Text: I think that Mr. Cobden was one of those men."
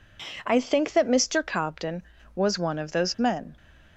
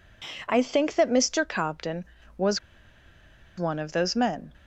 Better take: first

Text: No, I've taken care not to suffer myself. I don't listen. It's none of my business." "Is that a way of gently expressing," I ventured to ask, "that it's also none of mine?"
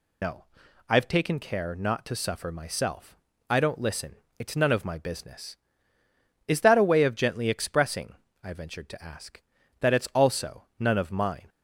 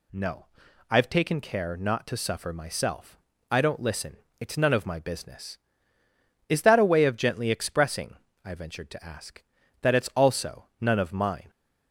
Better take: second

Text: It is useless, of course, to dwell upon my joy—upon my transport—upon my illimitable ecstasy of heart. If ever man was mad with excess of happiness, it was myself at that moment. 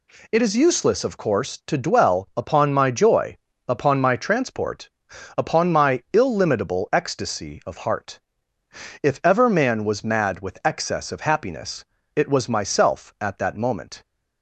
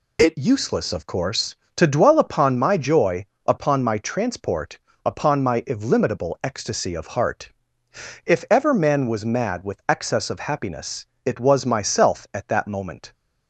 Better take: first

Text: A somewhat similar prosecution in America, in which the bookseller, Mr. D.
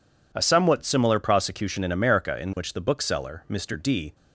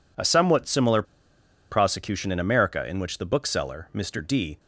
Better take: first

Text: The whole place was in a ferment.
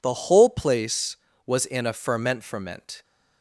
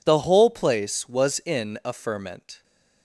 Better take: second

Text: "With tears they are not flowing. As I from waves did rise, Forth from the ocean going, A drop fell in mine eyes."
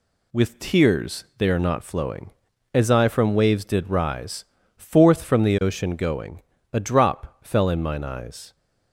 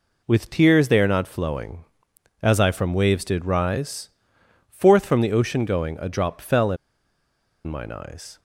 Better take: first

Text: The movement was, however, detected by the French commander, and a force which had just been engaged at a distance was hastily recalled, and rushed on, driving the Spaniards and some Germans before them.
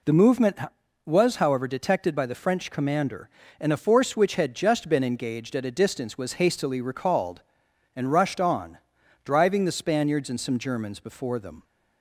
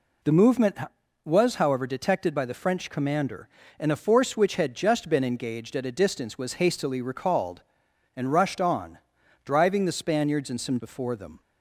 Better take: first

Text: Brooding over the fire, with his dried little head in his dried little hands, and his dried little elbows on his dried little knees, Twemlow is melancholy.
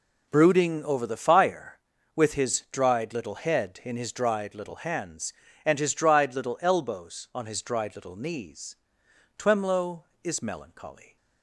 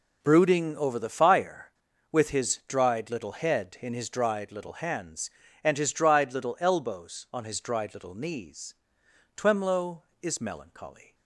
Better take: neither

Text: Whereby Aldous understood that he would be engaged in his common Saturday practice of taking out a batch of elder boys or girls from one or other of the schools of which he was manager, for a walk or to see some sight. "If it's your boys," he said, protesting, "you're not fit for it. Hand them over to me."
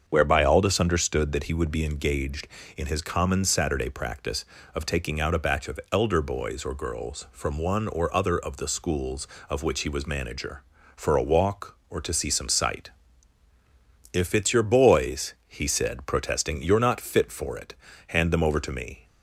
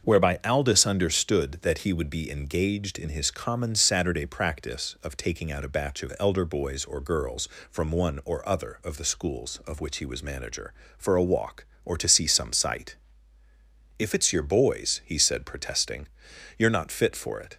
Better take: first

